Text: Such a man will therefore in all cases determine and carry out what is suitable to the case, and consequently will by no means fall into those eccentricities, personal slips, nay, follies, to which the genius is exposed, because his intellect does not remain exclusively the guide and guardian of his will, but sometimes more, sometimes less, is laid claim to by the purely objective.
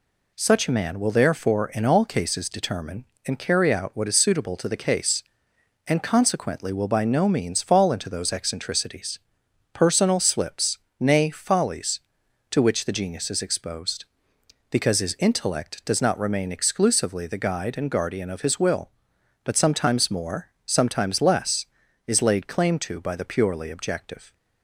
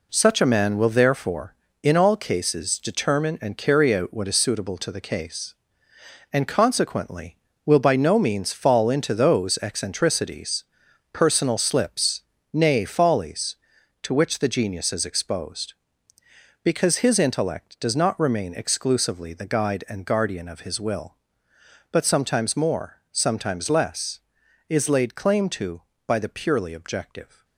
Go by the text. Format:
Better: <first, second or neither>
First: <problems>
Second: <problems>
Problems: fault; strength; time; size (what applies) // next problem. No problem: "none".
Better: first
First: none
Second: gets quieter; strong; throughout; 7.5 dB